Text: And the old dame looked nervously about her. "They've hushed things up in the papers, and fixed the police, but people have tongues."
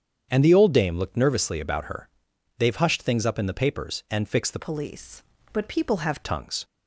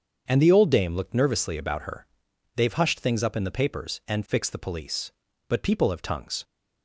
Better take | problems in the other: second | starts louder than the rest; strong; until 1.3 s; 8 dB; strong in the second // changes voice from "police" to "have"; from 4.5 to 6.2 s; 1.7 s long

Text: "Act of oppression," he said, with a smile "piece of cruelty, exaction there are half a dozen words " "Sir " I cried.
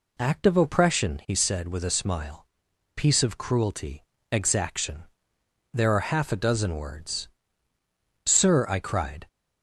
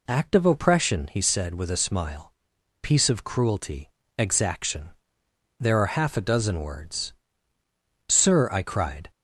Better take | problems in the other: neither | pauses between "smile" and "piece"; noticeable; the same in both // pauses between "exaction" and "there"; noticeable; the same in both

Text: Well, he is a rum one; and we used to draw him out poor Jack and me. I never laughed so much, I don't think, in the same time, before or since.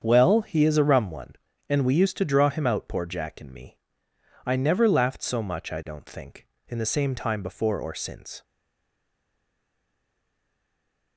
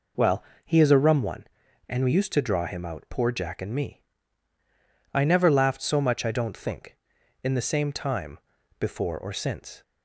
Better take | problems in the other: second | starts louder than the rest; strong; until 1.0 s; 7.5 dB // stays silent after the last word; strong; from 8.4 s on; 2.7 s long

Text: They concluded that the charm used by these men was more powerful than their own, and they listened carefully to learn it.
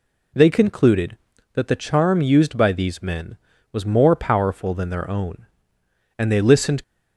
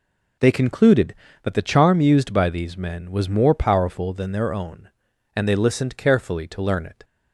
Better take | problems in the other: second | stops before "carefully to learn it"; at 6.8 s

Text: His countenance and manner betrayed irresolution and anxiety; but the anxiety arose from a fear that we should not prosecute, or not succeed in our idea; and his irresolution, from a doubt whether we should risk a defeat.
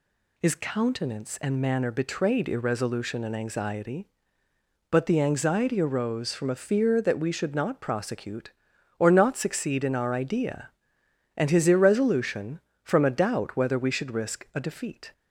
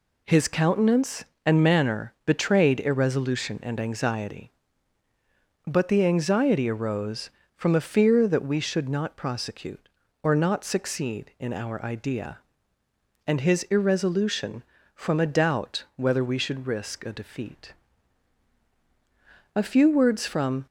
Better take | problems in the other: first | goes on to say "A few words from"; noticeable; from 19.4 s on; 1.1 s long

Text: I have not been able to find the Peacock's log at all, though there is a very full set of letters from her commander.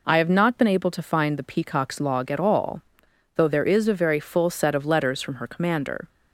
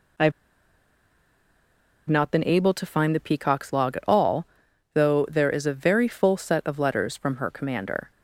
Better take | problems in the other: first | pauses between "have" and "not"; strong; at 0.3 s; 1.7 s long

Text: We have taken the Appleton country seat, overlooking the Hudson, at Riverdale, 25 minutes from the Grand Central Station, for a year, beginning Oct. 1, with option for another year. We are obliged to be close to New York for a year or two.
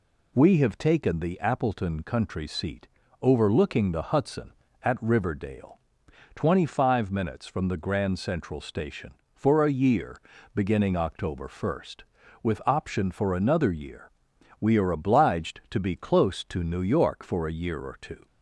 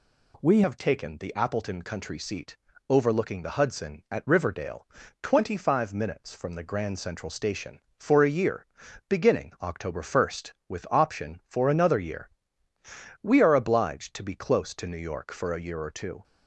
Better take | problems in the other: first | changes voice at "have"; from 0.6 s on; 15.6 s long

